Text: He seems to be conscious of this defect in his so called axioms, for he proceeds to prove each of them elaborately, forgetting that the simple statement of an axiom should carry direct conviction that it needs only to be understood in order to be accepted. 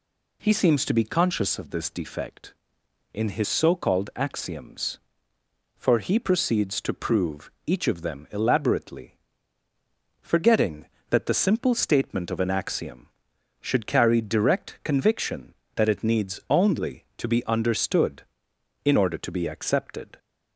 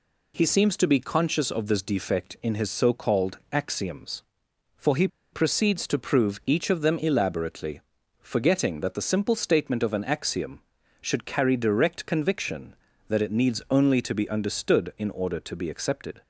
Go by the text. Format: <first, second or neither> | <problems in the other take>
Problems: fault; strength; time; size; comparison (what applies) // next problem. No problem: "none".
first | pauses between "called" and "axioms"; slight; at 3.3 s; 0.16 s long // pauses between "he" and "proceeds"; slight; at 5.0 s; 0.25 s long